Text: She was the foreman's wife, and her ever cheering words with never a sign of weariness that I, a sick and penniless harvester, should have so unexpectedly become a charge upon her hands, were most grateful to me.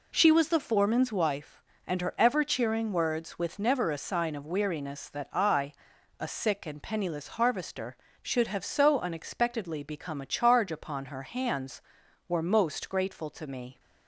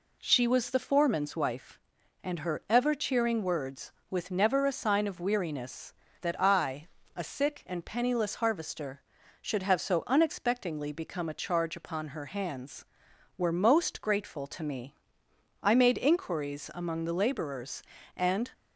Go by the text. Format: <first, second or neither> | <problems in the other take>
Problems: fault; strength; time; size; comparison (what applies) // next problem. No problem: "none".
first | goes on to say "I made inquiries among the laborers and"; strong; from 15.6 s on; 2.8 s long